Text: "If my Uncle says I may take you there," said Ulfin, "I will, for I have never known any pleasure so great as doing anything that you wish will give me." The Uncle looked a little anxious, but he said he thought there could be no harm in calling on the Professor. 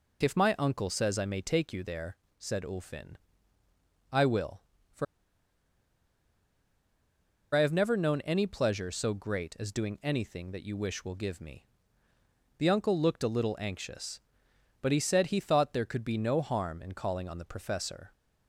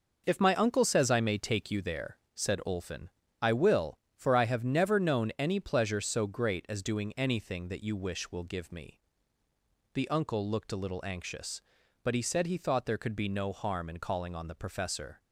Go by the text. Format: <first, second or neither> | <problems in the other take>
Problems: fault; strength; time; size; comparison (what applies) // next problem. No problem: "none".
second | pauses between "for" and "I"; strong; at 5.0 s; 2.4 s long